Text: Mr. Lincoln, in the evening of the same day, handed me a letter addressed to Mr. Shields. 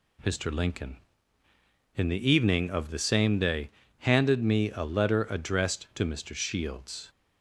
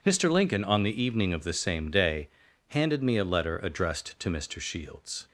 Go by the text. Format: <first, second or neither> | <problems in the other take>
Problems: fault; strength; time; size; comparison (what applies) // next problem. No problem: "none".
first | says "on" for "in"; at 0.6 s